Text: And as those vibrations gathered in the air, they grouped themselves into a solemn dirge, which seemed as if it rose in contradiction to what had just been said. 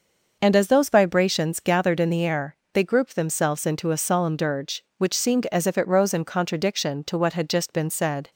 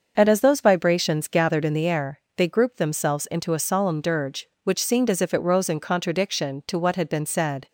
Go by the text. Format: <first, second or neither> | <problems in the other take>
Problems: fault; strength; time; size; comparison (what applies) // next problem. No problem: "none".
first | starts louder than the rest; until 1.1 s; 6.5 dB // skips "just"; at 7.0 s